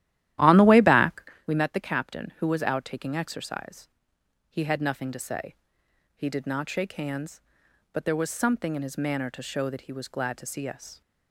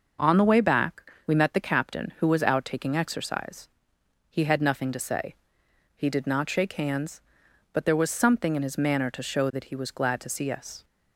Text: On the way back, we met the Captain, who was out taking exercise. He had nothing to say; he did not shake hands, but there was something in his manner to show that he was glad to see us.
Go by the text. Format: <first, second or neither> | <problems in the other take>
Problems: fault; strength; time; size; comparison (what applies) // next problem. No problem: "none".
second | starts louder than the rest; strong; until 1.5 s; 13 dB